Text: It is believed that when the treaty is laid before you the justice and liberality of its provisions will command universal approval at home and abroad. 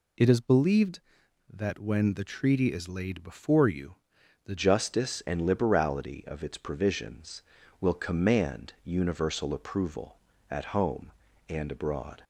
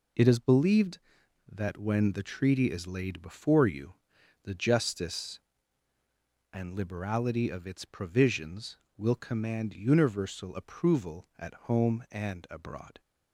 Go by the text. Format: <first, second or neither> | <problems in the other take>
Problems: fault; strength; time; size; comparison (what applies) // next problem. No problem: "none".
second | pauses between "you" and "the"; noticeable; at 3.9 s; 0.50 s long; noticeable in the second // changes voice at "justice"; from 4.5 s on; 7.7 s long